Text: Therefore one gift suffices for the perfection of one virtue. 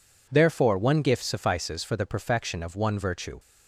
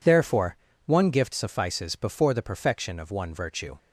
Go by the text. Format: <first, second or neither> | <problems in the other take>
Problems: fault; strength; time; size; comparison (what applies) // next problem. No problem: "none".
first | pauses between "Therefore" and "one"; slight; at 0.5 s; 0.28 s long // says "before" for "for"; at 1.9 s